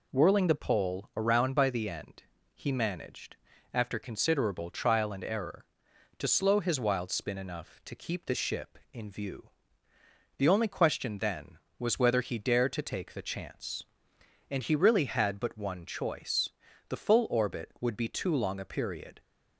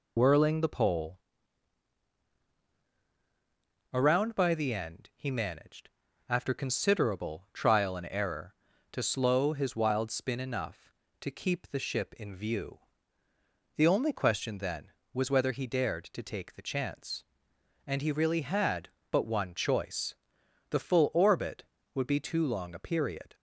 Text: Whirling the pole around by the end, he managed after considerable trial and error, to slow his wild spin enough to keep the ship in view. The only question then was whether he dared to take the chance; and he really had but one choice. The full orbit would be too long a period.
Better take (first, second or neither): first